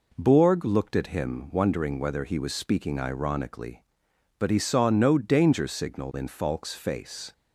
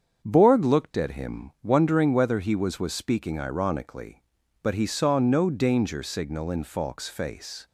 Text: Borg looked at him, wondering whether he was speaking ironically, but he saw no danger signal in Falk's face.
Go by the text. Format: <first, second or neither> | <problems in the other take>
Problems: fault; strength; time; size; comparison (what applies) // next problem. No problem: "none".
first | starts louder than the rest; strong; until 1.2 s; 7.5 dB // says "was" twice; at 2.7 s